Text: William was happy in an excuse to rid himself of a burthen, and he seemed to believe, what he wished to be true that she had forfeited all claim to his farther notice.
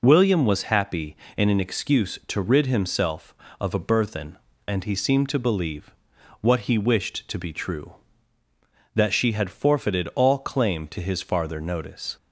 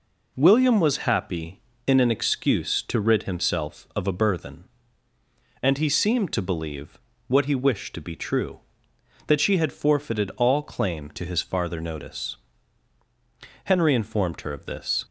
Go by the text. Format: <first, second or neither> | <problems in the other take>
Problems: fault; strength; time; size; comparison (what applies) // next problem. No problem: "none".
first | goes on to say "Henry informed her of this"; from 13.6 s on; 1.4 s long